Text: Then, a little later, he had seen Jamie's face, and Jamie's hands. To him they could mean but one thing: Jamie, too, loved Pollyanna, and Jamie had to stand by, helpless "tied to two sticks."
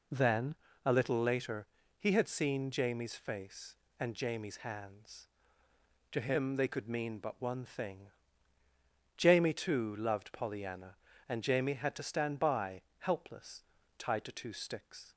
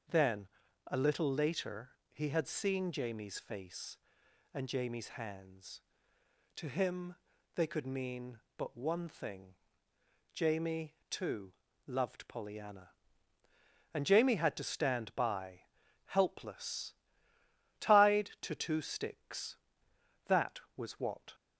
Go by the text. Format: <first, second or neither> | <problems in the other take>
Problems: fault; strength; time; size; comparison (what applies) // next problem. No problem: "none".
first | starts louder than the rest; until 1.4 s; 6.5 dB // pauses between "him" and "they"; at 7.1 s; 0.40 s long // pauses between "helpless" and "tied"; noticeable; at 16.9 s; 0.88 s long; slight in the first // goes on to say "That was what"; noticeable; from 20.2 s on; 1.0 s long